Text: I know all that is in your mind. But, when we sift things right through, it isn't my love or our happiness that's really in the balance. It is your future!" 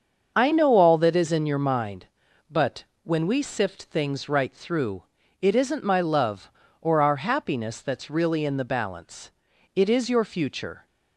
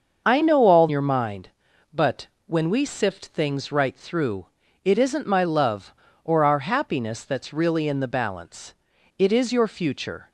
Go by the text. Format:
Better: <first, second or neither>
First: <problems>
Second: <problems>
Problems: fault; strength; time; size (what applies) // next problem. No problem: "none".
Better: first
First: starts louder than the rest; until 1.3 s; 6.5 dB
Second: starts louder than the rest; until 1.2 s; 6.5 dB // skips "that is in"; at 0.8 s